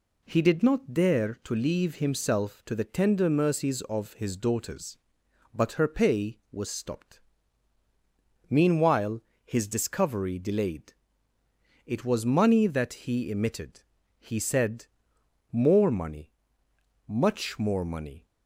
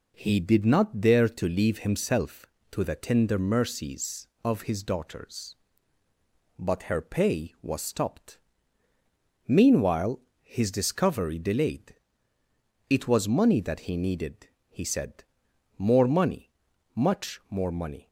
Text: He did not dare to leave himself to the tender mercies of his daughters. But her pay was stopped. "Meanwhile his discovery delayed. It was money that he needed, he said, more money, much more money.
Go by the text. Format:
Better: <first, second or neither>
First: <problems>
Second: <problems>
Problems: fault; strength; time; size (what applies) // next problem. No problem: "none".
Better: second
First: pauses between "Meanwhile" and "his"; slight; at 9.2 s; 0.24 s long // says "emitted" for "needed"; at 13.2 s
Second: pauses between "Meanwhile" and "his"; slight; at 10.2 s; 0.20 s long